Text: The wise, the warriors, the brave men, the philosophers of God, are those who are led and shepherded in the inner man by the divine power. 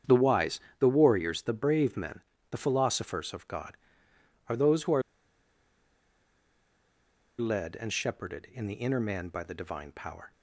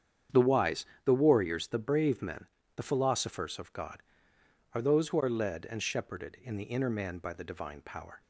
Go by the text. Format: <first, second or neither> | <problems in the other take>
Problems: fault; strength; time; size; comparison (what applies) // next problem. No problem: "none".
second | starts louder than the rest; strong; until 1.2 s; 8 dB; strong in the second // pauses between "are" and "led"; strong; at 5.0 s; 2.3 s long